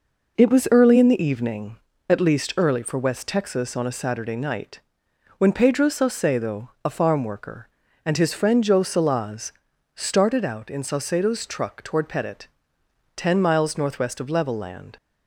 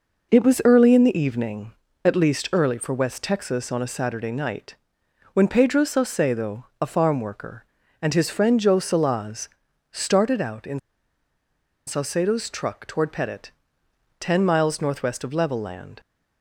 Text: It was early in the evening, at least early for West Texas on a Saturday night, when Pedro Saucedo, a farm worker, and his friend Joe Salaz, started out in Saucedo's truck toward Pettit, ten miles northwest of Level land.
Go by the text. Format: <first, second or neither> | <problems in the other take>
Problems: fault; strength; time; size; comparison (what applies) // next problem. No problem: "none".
first | pauses between "in" and "Saucedo's"; at 10.7 s; 1.0 s long